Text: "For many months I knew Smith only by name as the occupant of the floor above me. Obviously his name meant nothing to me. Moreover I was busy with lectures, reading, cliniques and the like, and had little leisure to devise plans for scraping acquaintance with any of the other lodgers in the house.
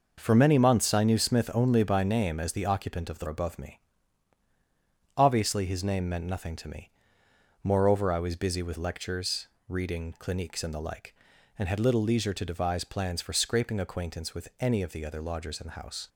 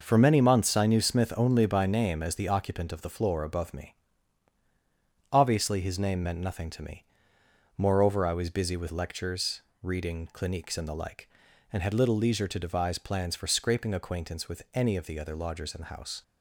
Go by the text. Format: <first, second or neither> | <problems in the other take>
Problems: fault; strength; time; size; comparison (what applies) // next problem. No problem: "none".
second | skips "floor"; at 3.2 s